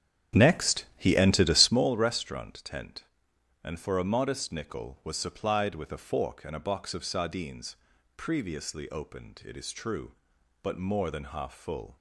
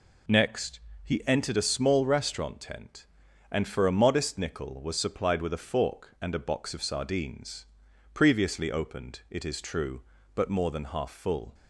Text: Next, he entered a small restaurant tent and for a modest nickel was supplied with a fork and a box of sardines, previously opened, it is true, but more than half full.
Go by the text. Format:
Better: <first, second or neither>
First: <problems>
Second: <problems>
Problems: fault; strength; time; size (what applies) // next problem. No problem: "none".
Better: second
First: starts louder than the rest; strong; until 1.8 s; 9 dB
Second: none